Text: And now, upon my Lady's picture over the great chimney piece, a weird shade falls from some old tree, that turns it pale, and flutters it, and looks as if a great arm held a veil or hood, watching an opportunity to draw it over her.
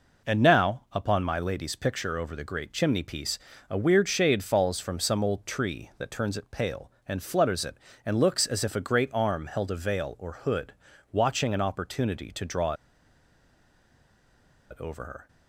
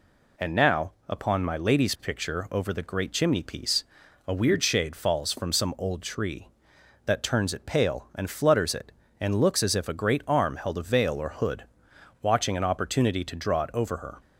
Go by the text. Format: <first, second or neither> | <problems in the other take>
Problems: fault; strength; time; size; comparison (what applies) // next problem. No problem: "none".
second | pauses between "draw" and "it"; strong; at 12.7 s; 1.9 s long